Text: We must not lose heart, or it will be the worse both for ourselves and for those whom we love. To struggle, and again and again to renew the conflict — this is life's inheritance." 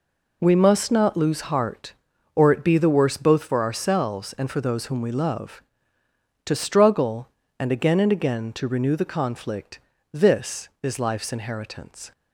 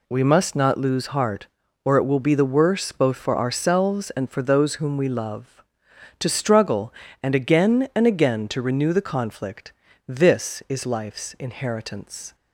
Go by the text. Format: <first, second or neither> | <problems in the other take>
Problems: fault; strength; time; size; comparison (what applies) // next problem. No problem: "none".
second | skips "will"; at 2.6 s